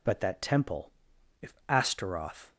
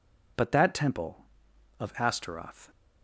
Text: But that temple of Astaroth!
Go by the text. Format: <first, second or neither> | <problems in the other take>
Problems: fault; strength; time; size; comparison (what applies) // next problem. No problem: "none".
second | says "if" for "of"; at 1.4 s